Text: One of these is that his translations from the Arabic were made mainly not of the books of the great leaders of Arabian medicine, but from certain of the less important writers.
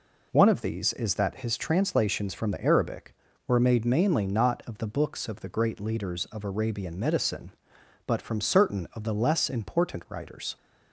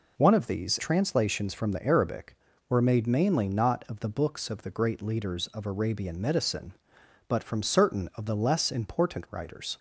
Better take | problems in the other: first | skips "is that his"; at 0.7 s

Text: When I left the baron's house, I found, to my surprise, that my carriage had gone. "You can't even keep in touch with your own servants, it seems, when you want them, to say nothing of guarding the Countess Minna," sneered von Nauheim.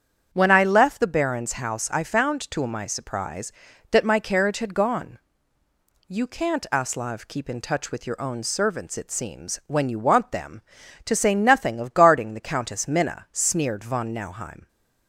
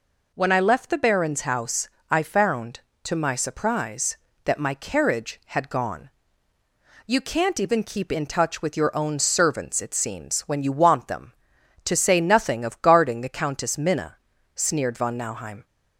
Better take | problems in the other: second | starts louder than the rest; strong; until 1.3 s; 8 dB // says "aslav" for "even"; at 6.7 s

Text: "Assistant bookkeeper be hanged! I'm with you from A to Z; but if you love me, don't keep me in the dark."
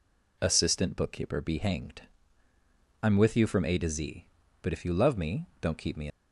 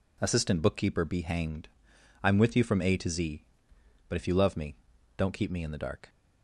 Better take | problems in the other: second | stops before "in the dark"; at 6.0 s

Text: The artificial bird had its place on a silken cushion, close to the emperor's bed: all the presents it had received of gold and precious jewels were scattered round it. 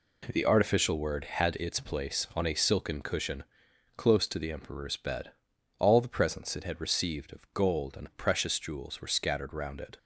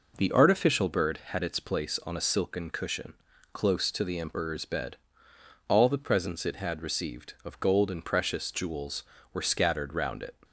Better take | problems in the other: second | says "word" for "bird"; at 0.9 s

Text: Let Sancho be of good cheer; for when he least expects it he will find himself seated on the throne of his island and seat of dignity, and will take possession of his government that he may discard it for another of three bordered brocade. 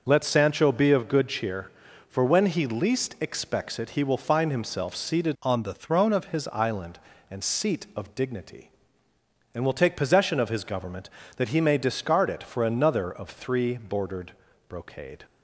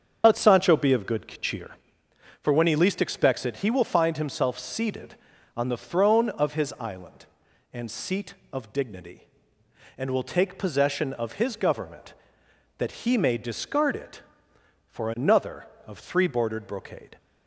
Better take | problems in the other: second | starts louder than the rest; noticeable; until 1.0 s; 6 dB; also in the second // changes voice from "on" to "of"; from 5.4 to 6.2 s; 0.8 s long // pauses between "bordered" and "brocade"; at 14.3 s; 0.38 s long

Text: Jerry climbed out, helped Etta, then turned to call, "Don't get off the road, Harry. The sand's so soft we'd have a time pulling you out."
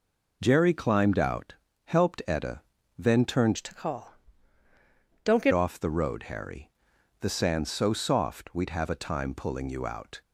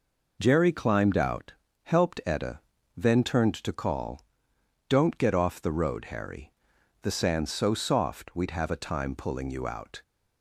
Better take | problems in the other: second | changes voice from "to" to "get"; from 3.5 to 5.5 s; 2.0 s long

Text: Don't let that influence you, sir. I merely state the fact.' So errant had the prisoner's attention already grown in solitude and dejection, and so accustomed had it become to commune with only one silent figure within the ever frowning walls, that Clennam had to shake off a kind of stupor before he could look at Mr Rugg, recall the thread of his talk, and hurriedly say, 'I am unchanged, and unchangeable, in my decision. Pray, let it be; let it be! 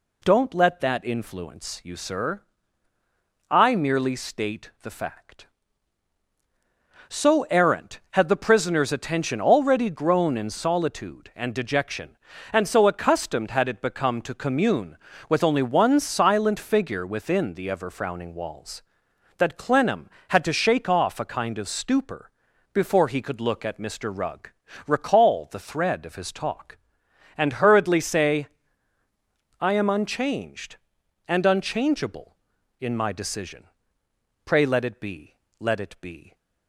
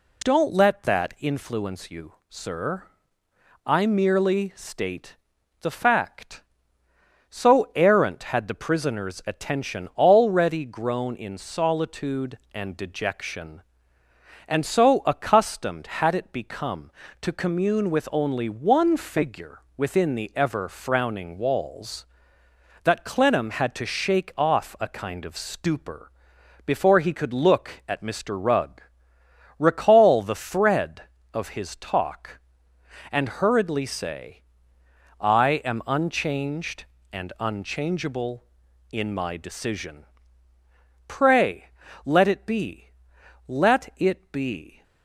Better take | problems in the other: first | pauses between "state" and "the"; at 5.1 s; 0.44 s long // skips "silent"; at 18.9 s // pauses between "figure" and "within"; slight; at 19.6 s; 0.18 s long // pauses between "stupor" and "before"; noticeable; at 26.1 s; 0.56 s long; also in the first

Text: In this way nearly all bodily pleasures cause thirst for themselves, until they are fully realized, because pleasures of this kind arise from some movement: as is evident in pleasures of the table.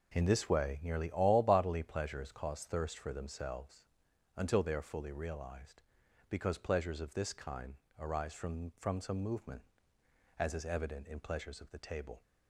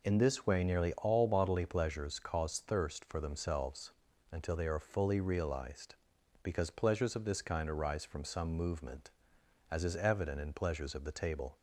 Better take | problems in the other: second | pauses between "kind" and "arise"; slight; at 7.7 s; 0.24 s long // says "from" twice; at 8.7 s

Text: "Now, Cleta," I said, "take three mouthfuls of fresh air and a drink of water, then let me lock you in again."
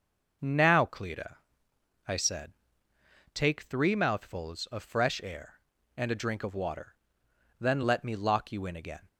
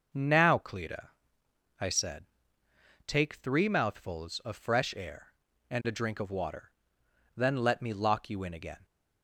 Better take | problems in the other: neither | none

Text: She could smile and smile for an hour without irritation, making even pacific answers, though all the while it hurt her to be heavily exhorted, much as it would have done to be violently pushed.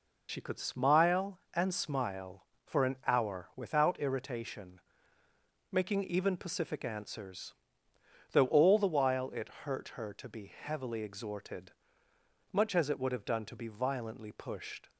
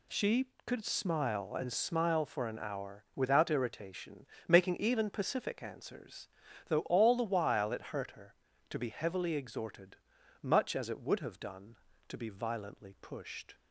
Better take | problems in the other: second | loses the start of "She"; at 0.2 s; 60 ms

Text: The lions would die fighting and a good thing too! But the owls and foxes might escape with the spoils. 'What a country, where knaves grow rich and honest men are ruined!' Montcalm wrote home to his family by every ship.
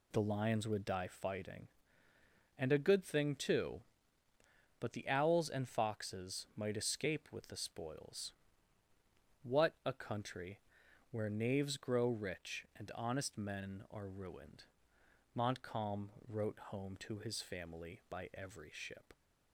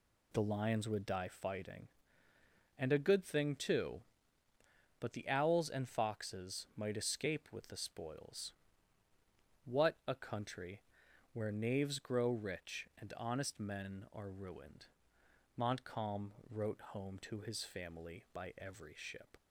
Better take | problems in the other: neither | pauses between "Montcalm" and "wrote"; slight; the same in both

